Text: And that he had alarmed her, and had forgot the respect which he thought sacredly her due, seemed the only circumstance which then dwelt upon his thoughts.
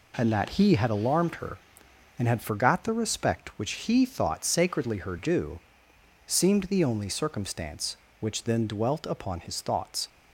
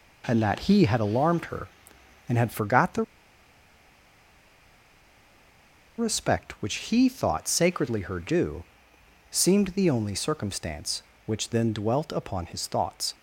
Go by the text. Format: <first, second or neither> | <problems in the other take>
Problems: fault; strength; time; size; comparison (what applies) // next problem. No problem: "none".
first | pauses between "the" and "respect"; strong; at 3.0 s; 2.9 s long